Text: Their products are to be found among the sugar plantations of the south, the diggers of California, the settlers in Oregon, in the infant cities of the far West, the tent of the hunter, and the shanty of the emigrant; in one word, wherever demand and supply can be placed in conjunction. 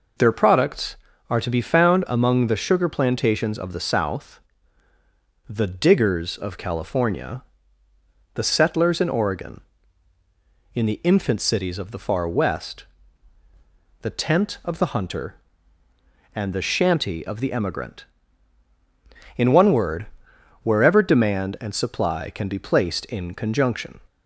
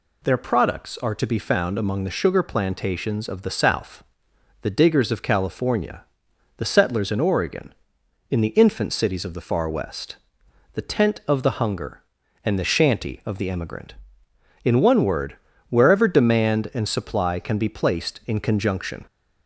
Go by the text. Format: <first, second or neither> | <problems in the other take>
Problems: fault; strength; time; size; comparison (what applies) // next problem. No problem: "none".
first | says "hunger" for "hunter"; at 11.5 s